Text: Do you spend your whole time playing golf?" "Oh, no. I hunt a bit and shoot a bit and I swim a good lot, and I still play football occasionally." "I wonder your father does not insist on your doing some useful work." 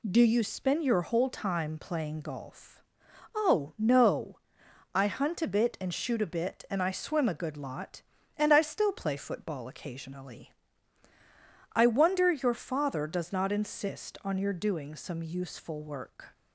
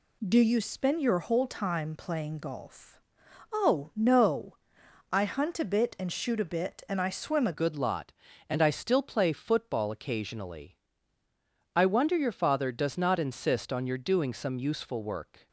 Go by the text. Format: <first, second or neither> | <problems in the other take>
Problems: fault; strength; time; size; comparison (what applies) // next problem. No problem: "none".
first | changes voice at "good"; from 7.5 s on; 7.9 s long